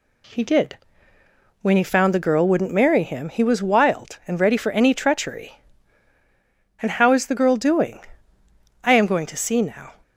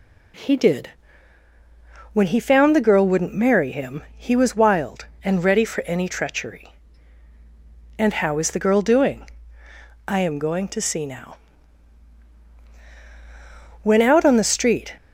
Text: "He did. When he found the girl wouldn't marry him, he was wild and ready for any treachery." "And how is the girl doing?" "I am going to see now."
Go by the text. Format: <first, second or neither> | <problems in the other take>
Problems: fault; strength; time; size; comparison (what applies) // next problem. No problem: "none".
first | goes on to say "When out on the street"; noticeable; from 13.8 s on; 1.1 s long